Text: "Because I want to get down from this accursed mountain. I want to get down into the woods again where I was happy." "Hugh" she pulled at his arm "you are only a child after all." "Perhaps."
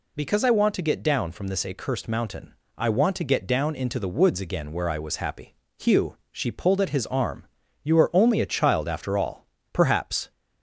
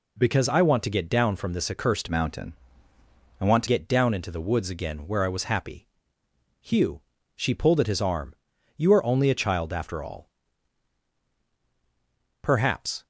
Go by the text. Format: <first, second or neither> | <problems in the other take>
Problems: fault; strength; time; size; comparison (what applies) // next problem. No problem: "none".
first | changes voice from "mountain" to "to"; from 2.0 to 3.6 s; 1.6 s long // pauses between "Hugh" and "she"; slight; at 6.9 s; 0.34 s long; slight in the first // pauses between "arm" and "you"; at 8.3 s; 0.40 s long; slight in the first